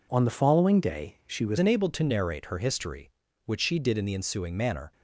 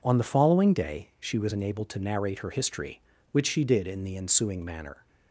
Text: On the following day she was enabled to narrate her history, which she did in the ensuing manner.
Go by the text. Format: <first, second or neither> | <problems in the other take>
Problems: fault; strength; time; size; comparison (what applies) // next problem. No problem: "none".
second | changes voice at "enabled"; from 1.5 s on; 3.4 s long